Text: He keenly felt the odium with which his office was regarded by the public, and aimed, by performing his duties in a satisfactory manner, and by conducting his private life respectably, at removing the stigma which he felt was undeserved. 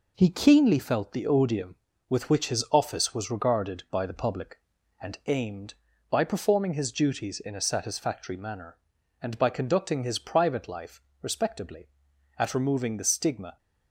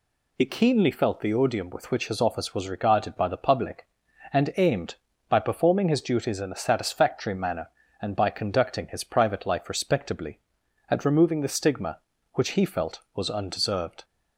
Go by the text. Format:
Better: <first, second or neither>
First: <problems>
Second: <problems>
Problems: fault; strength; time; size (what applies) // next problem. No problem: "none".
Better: second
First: pauses between "life" and "respectably"; slight; at 11.0 s; 0.20 s long // stops before "which he felt was undeserved"; at 13.5 s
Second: none